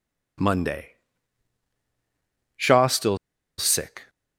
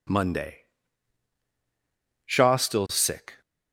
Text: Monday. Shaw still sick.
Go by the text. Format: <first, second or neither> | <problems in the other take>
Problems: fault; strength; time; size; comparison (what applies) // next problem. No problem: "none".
second | pauses between "still" and "sick"; at 3.1 s; 0.41 s long